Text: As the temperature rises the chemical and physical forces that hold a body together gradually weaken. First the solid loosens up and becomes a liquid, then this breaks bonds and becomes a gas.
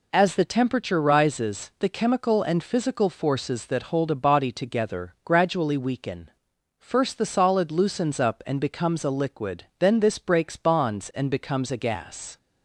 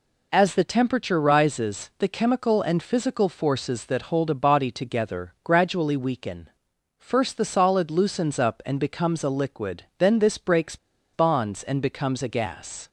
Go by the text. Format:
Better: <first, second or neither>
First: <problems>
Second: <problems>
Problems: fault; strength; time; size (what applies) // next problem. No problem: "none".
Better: first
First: none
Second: pauses between "breaks" and "bonds"; at 10.7 s; 0.37 s long